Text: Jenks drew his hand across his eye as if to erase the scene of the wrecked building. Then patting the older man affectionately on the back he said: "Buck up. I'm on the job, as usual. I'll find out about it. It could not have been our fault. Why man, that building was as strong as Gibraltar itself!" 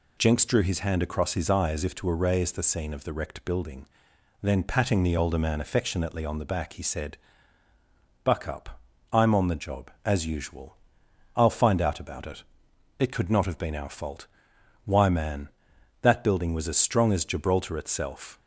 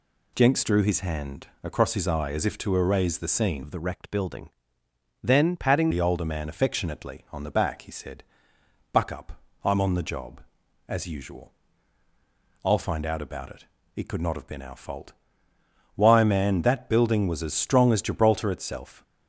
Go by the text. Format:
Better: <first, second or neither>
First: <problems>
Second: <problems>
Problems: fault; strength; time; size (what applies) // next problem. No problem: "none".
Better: first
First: none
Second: pauses between "hand" and "across"; slight; at 1.4 s; 0.16 s long // changes voice from "of" to "patting"; from 3.6 to 5.9 s; 2.3 s long